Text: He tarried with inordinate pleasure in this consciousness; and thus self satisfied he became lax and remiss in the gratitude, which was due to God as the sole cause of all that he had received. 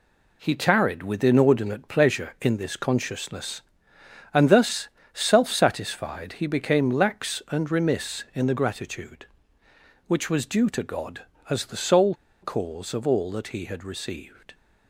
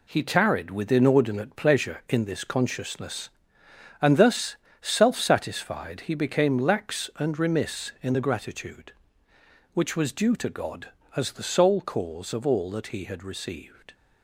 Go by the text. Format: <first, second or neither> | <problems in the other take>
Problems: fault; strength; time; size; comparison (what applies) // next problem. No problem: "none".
second | pauses between "thus" and "self"; slight; at 4.8 s; 0.26 s long; slight in the second // pauses between "sole" and "cause"; slight; at 12.1 s; 0.29 s long